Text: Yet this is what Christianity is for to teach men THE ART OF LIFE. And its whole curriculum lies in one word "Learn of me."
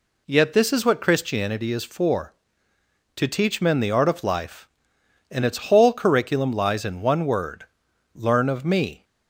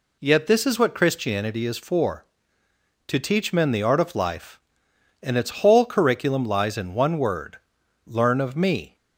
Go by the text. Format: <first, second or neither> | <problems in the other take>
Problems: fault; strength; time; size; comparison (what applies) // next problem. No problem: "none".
neither | pauses between "word" and "Learn"; noticeable; the same in both